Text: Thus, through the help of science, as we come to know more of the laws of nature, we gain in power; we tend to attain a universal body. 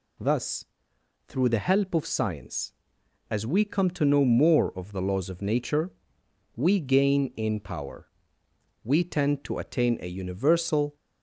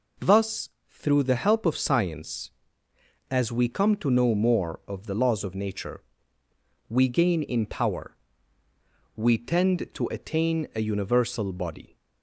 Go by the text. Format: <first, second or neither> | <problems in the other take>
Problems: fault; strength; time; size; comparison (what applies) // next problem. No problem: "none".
second | stops before "body"; at 10.9 s